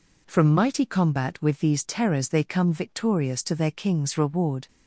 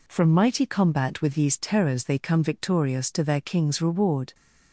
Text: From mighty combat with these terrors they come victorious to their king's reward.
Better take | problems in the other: neither | none

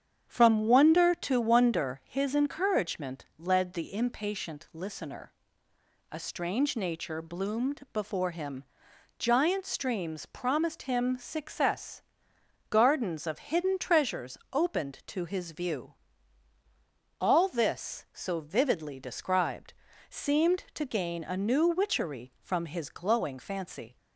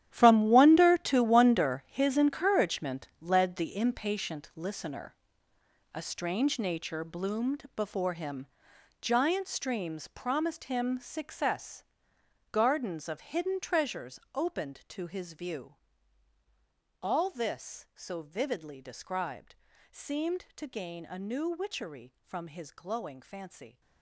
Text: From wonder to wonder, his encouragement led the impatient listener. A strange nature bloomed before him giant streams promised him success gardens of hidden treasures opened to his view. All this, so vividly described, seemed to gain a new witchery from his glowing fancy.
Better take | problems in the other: first | gets quieter; strong; throughout; 15 dB // starts louder than the rest; strong; until 1.1 s; 11 dB; strong in the first // pauses between "him" and "giant"; noticeable; at 8.4 s; 0.54 s long; noticeable in the first // pauses between "success" and "gardens"; noticeable; at 11.8 s; 0.68 s long; noticeable in the first // pauses between "treasures" and "opened"; slight; at 14.1 s; 0.16 s long; slight in the first

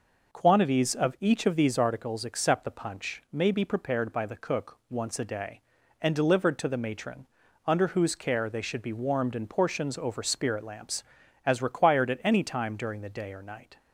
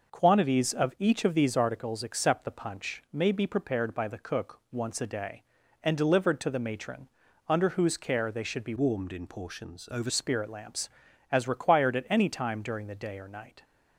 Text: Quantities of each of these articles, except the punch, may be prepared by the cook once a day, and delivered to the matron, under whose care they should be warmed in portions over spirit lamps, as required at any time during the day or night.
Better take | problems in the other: first | changes voice from "warmed" to "over"; from 8.7 to 10.1 s; 1.4 s long

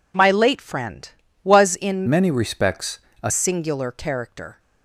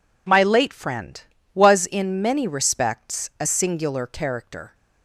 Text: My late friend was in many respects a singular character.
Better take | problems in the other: second | changes voice from "many" to "a"; from 2.0 to 3.3 s; 1.3 s long // pauses between "respects" and "a"; slight; at 2.9 s; 0.24 s long

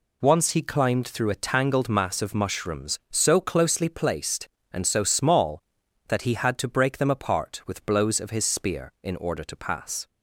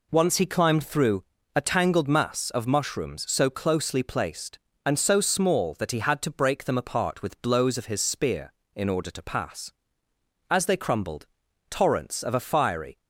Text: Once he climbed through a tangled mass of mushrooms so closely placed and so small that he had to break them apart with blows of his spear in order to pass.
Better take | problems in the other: first | pauses between "through" and "a"; slight; at 1.2 s; 0.32 s long // goes on to say "As they crumbled torrents of a fiery"; strong; from 10.4 s on; 2.5 s long

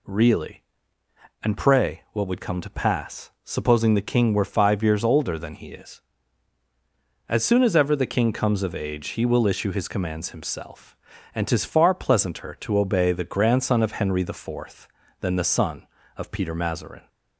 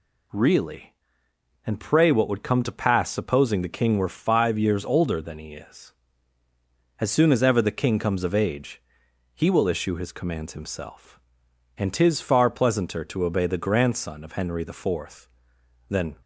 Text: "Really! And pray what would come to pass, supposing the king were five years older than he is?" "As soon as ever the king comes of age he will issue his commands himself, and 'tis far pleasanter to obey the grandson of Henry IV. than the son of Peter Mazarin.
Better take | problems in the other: first | pauses between "age" and "he"; noticeable; at 8.8 s; 0.54 s long // stops before "the son of Peter Mazarin"; at 16.2 s

